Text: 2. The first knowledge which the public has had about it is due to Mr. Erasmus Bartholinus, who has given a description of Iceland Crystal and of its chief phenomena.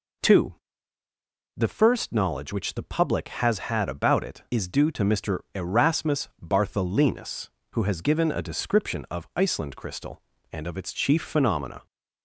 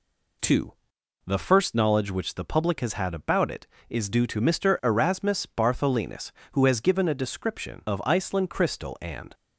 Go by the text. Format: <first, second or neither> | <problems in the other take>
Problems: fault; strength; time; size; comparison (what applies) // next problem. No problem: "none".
first | stops before "of its chief phenomena"; at 9.3 s